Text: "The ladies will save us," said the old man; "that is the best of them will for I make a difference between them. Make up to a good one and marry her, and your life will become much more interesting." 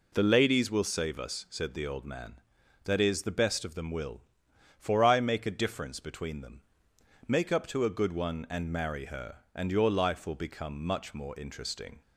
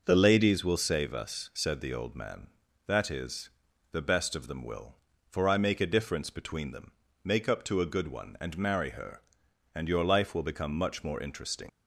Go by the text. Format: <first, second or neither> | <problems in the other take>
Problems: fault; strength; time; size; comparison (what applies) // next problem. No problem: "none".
first | pauses between "is" and "the"; at 3.4 s; 0.44 s long // leaves "interesting" unfinished; at 11.6 s; 100 ms